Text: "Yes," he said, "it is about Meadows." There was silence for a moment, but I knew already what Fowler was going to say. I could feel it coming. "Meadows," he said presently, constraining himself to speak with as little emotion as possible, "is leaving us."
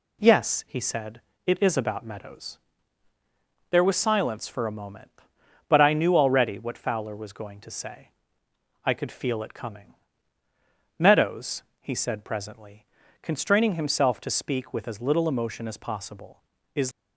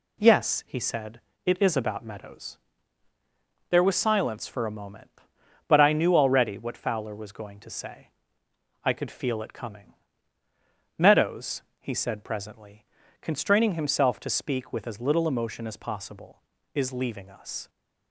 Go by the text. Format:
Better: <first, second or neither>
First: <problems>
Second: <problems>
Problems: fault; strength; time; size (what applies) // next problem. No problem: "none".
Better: second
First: stops before "leaving us"; at 16.9 s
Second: none